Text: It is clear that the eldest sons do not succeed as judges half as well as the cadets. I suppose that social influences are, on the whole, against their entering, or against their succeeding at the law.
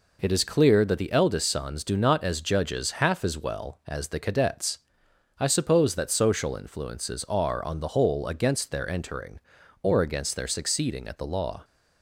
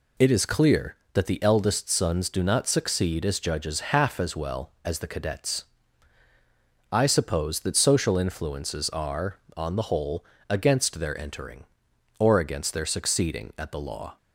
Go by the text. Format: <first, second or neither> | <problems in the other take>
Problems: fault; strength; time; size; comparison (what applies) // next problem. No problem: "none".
second | skips "succeed"; at 2.2 s